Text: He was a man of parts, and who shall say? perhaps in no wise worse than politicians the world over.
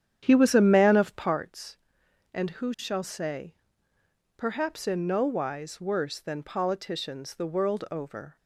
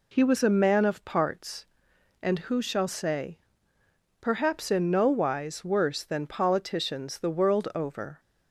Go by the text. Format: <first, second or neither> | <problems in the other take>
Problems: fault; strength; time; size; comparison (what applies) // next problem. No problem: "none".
second | starts louder than the rest; strong; until 1.3 s; 9.5 dB